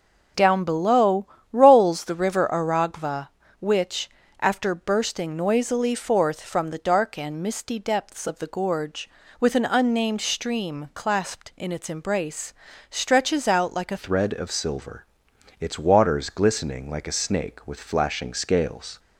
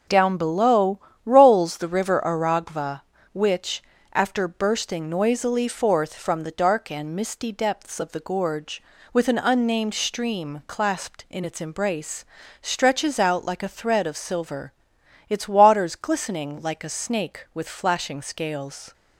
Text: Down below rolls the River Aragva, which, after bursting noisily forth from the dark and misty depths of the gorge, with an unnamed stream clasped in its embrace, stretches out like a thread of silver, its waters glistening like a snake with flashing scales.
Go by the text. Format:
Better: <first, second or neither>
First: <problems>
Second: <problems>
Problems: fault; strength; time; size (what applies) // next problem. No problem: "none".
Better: second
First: starts louder than the rest; until 1.6 s; 6.5 dB // pauses between "below" and "rolls"; slight; at 1.2 s; 0.28 s long // changes voice at "thread"; from 13.9 s on; 5.0 s long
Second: starts louder than the rest; until 1.3 s; 6.5 dB // pauses between "below" and "rolls"; slight; at 0.9 s; 0.28 s long